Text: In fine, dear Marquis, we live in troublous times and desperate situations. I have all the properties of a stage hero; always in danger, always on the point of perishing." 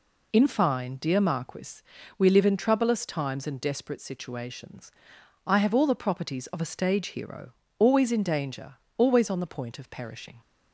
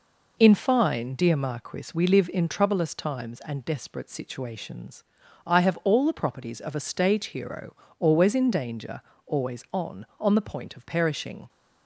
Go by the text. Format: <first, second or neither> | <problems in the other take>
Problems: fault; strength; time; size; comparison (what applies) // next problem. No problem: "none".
first | says "on" twice; at 10.1 s